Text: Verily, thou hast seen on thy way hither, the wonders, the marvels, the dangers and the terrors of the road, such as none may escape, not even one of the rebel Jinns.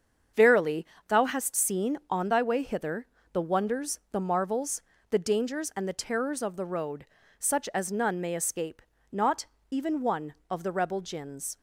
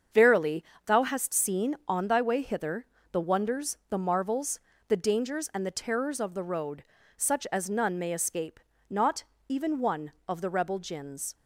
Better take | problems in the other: neither | starts louder than the rest; the same in both // pauses between "not" and "even"; slight; the same in both

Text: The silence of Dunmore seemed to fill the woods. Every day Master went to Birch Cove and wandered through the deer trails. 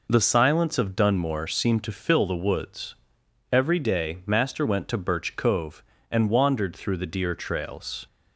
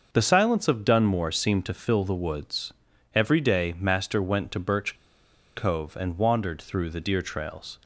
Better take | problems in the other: first | starts louder than the rest; until 1.1 s; 6.5 dB // pauses between "Birch" and "Cove"; noticeable; at 4.9 s; 0.58 s long

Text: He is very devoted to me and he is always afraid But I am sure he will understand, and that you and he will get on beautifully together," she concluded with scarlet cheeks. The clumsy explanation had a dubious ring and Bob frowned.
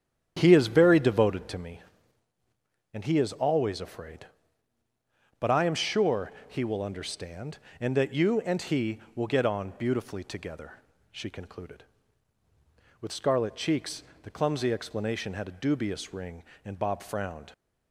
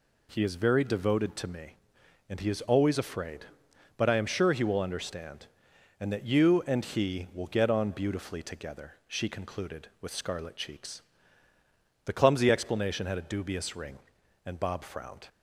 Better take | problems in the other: second | starts louder than the rest; strong; until 1.6 s; 9 dB // pauses between "sure" and "he"; slight; at 6.3 s; 0.16 s long

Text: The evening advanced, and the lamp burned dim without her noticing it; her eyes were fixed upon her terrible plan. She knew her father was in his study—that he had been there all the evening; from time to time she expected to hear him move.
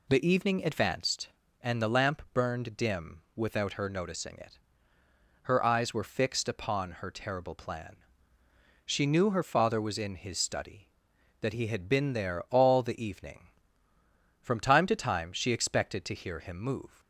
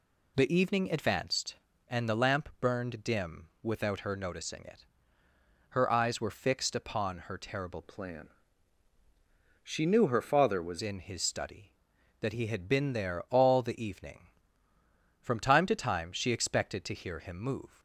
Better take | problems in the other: first | pauses between "dim" and "without"; slight; at 3.4 s; 0.16 s long; slight in the first // changes voice from "plan" to "was"; from 7.8 to 10.7 s; 2.9 s long

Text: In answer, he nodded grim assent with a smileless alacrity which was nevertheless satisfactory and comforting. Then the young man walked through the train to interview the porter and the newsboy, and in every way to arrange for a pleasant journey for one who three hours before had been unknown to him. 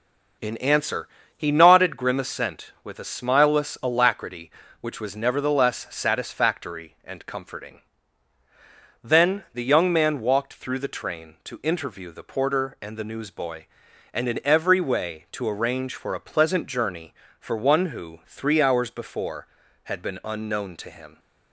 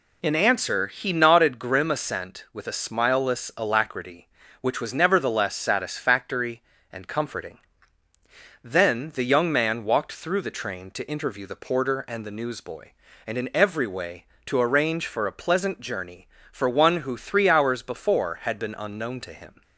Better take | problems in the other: neither | none

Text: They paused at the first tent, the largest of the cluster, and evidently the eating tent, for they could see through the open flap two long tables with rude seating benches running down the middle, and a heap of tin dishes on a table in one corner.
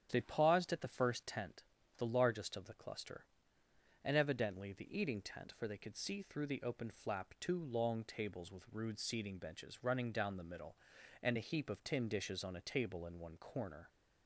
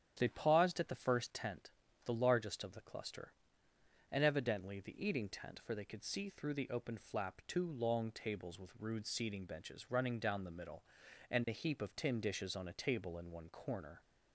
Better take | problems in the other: neither | starts louder than the rest; strong; the same in both

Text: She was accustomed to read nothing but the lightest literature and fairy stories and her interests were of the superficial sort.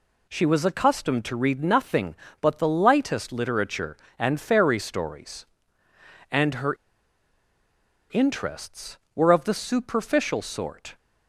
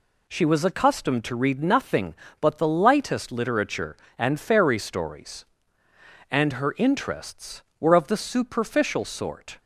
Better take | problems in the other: second | pauses between "her" and "interests"; strong; at 6.7 s; 1.3 s long

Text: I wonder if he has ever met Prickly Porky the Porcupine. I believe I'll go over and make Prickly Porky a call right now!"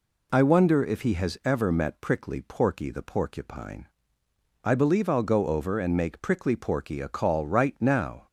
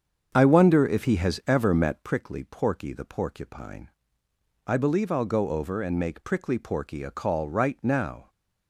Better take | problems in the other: first | starts louder than the rest; strong; until 2.1 s; 7.5 dB

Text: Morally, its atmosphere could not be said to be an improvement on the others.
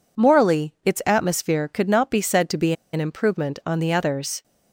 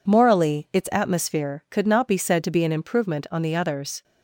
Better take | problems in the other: second | pauses between "be" and "an"; slight; at 2.7 s; 0.20 s long

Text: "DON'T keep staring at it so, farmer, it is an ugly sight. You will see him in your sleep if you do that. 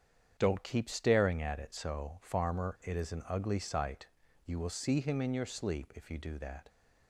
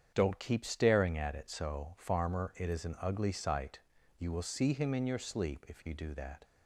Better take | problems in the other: neither | starts louder than the rest; strong; the same in both

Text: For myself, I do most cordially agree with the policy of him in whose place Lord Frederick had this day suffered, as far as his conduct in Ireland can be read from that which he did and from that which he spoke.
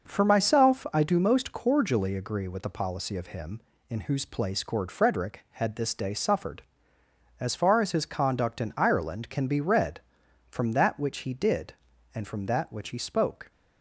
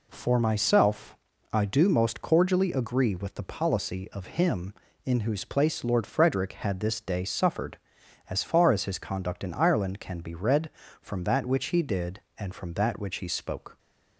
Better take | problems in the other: second | says "Cord" for "Lord"; at 4.6 s

